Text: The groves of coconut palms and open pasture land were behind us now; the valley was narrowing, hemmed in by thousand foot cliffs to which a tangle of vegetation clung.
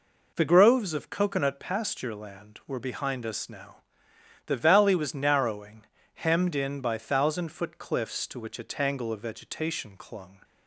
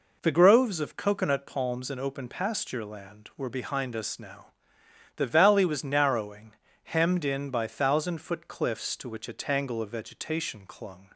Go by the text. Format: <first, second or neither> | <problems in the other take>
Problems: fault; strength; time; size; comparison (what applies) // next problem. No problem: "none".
second | skips "palms and open"; at 1.5 s